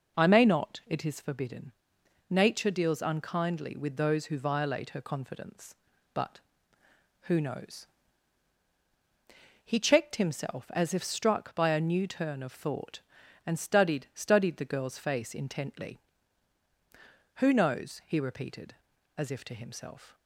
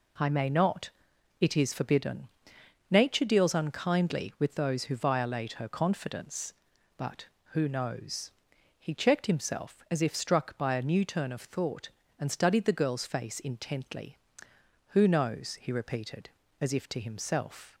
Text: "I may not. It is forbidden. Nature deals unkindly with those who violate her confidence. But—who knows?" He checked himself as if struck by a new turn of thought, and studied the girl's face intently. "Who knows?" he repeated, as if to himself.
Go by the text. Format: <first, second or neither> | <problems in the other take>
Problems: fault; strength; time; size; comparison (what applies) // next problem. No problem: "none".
second | says "studied" twice; at 14.1 s